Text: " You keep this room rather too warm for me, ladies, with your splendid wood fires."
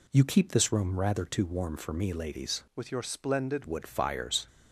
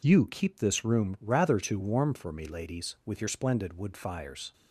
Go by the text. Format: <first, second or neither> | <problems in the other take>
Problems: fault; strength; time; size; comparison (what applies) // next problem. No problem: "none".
second | changes voice from "with" to "splendid"; from 2.7 to 3.6 s; 0.9 s long